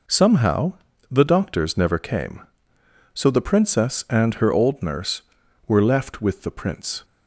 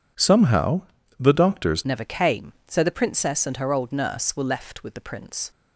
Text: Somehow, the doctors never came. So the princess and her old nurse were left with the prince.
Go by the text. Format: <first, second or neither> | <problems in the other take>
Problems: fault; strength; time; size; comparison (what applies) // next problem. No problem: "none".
first | changes voice at "never"; from 1.8 s on; 3.7 s long